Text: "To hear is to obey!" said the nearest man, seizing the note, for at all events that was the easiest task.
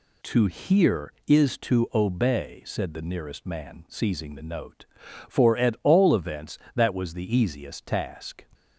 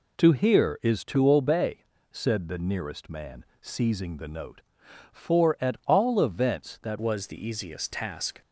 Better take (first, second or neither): first